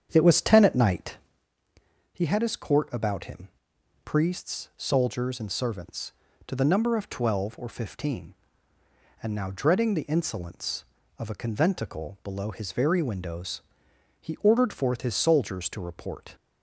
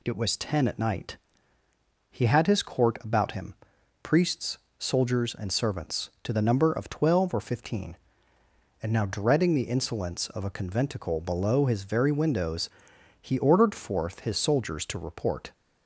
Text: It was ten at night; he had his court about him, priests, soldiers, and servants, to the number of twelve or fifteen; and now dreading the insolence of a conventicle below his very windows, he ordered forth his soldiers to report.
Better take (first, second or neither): second